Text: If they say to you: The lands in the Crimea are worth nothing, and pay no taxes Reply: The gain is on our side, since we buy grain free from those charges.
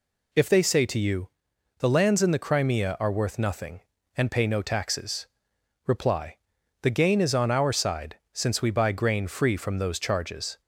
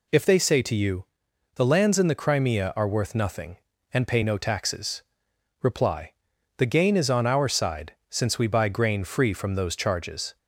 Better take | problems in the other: neither | pauses between "taxes" and "Reply"; noticeable; the same in both

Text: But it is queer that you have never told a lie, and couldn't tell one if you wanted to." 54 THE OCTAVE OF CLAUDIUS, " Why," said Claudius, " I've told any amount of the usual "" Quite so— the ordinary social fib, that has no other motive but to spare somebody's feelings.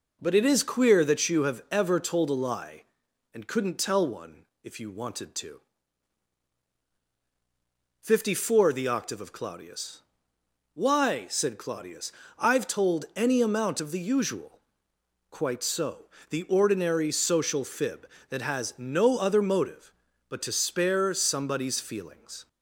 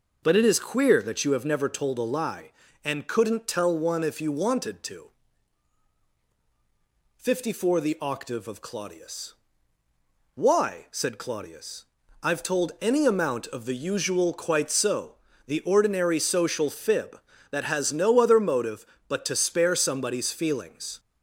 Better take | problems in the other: second | says "ever" for "never"; at 1.7 s // pauses between "one" and "if"; slight; at 4.4 s; 0.18 s long

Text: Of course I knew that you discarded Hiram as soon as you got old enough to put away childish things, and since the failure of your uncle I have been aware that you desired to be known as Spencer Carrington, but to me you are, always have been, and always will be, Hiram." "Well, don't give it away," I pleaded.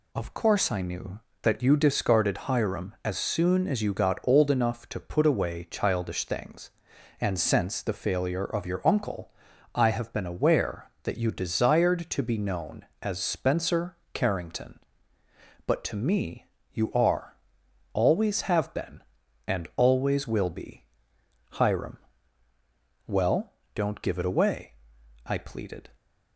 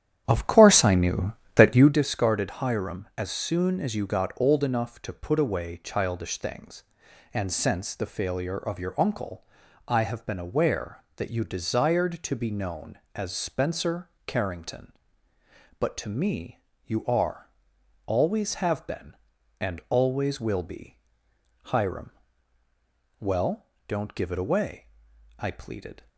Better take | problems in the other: first | starts louder than the rest; strong; until 2.0 s; 10 dB // pauses between "uncle" and "I"; at 9.4 s; 0.42 s long; also in the first // pauses between "Spencer" and "Carrington"; slight; at 14.0 s; 0.16 s long; slight in the first // pauses between "me" and "you"; slight; at 16.5 s; 0.30 s long; slight in the first

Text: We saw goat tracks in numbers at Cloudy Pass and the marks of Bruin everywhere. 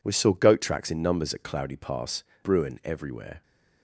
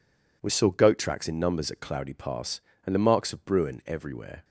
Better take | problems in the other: second | skips "and the marks of"; at 2.3 s

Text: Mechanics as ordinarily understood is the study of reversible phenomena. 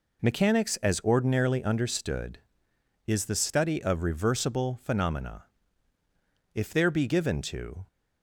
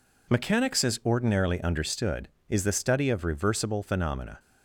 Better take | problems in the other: second | goes on to say "If there be given to"; from 6.5 s on; 1.3 s long

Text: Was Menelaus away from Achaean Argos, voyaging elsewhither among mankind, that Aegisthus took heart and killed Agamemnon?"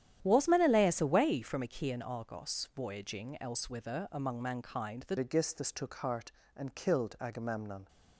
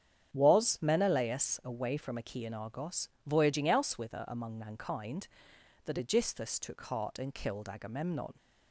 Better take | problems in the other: second | starts louder than the rest; strong; until 1.2 s; 10.5 dB; strong in the second // changes voice at "Aegisthus"; from 5.1 s on; 2.7 s long

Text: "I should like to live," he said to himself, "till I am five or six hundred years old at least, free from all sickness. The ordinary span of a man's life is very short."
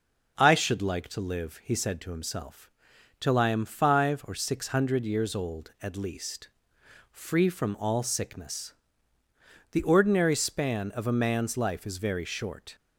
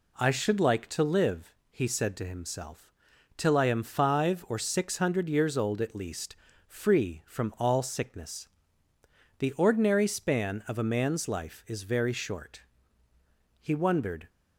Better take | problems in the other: first | goes on to say "He wondered"; noticeable; from 13.6 s on; 0.68 s long

